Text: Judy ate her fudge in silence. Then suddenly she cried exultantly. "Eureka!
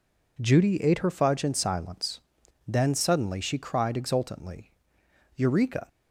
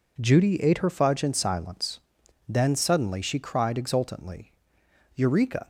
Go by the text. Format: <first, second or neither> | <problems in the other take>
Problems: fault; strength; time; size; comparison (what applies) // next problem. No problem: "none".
neither | none